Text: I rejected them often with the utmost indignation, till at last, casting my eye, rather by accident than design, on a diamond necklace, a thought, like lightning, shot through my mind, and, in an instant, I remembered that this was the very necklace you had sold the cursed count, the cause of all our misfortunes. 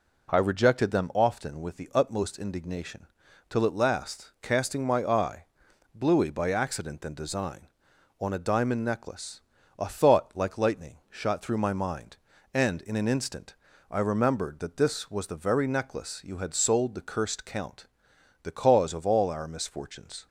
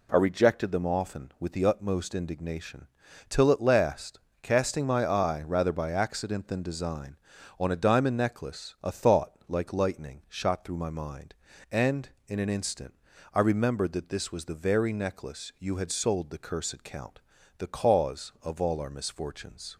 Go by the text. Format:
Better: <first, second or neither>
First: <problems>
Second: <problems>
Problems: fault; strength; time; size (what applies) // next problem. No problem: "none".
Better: second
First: says "bluey" for "rather"; at 5.9 s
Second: none